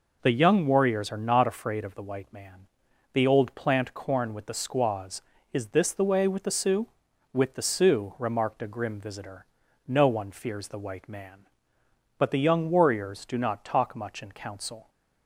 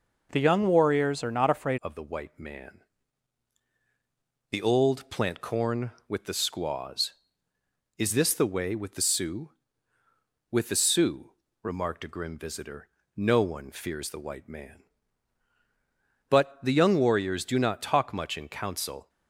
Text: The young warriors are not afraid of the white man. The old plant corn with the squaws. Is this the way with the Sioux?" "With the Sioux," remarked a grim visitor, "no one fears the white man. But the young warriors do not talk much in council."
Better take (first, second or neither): first